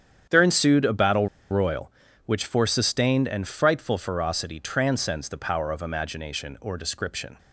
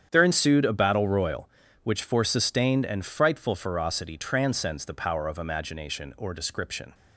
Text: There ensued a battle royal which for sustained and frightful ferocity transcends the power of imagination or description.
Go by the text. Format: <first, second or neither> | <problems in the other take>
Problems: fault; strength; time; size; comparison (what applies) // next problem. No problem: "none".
second | starts louder than the rest; strong; until 1.5 s; 8.5 dB; strong in the second // pauses between "battle" and "royal"; slight; at 1.2 s; 0.23 s long